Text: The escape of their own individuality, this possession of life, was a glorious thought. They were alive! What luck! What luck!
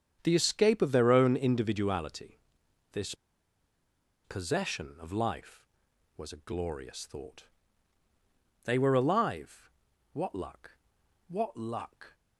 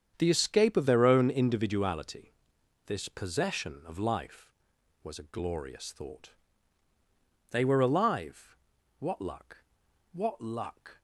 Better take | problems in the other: second | starts louder than the rest; strong; until 1.2 s; 8 dB; strong in the second // pauses between "this" and "possession"; at 3.1 s; 1.1 s long

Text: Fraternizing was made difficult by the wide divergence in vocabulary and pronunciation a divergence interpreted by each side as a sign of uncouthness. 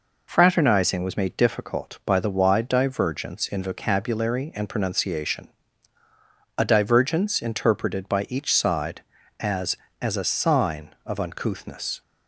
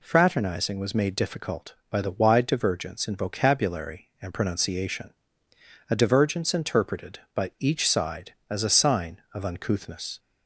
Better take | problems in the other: second | pauses between "pronunciation" and "a"; at 5.4 s; 1.1 s long; noticeable in the second // says "as" twice; at 10.0 s

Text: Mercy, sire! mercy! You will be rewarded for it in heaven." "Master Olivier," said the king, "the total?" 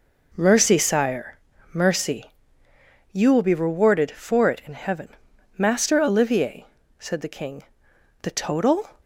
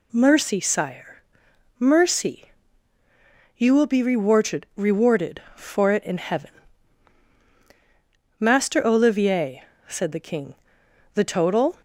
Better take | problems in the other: first | says "rewarded" twice; at 4.7 s

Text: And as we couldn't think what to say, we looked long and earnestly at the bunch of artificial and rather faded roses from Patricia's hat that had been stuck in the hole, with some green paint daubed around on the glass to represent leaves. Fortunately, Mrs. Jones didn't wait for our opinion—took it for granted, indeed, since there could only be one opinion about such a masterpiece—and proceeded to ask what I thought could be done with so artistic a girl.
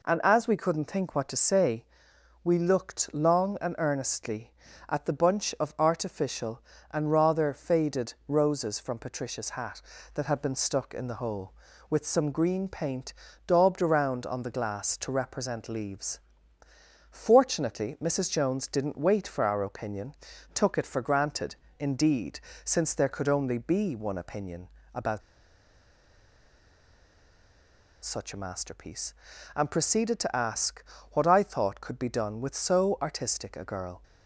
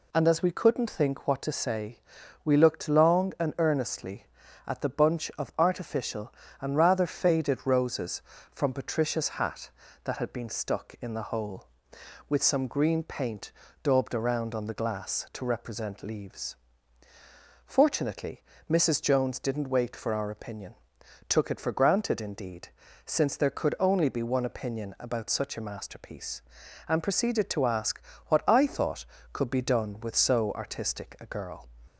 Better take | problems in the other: second | pauses between "paint" and "daubed"; slight; at 13.1 s; 0.32 s long; slight in the second // pauses between "opinion" and "about"; slight; at 24.6 s; 0.26 s long // pauses between "about" and "such"; strong; at 25.2 s; 2.8 s long // pauses between "ask" and "what"; slight; at 30.8 s; 0.30 s long; slight in the second

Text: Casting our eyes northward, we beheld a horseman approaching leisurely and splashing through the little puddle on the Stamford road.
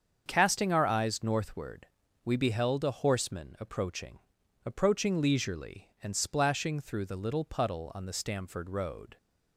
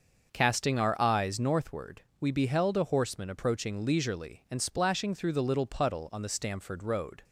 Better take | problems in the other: second | starts louder than the rest; until 1.2 s; 7 dB; also in the second // says "approaching" twice; at 4.6 s

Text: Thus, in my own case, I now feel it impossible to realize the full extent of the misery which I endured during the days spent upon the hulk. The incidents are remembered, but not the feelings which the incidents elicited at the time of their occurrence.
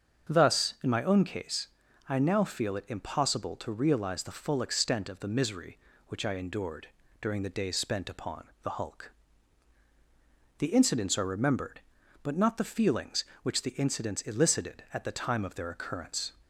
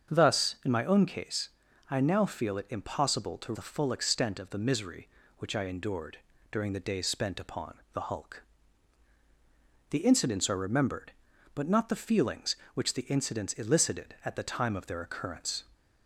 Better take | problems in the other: first | starts louder than the rest; until 1.2 s; 7 dB; also in the first // skips "realize"; at 3.5 s // pauses between "endured" and "during"; slight; at 6.1 s; 0.34 s long; slight in the first

